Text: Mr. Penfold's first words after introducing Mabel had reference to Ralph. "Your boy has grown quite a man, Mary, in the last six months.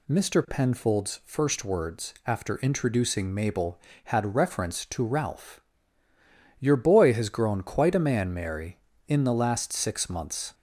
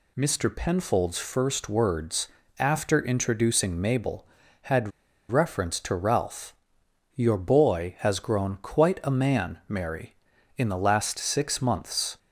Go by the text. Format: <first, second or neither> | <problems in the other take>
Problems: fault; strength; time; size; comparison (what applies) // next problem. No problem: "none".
first | pauses between "words" and "after"; slight; at 2.2 s; 0.32 s long // pauses between "had" and "reference"; at 4.9 s; 0.40 s long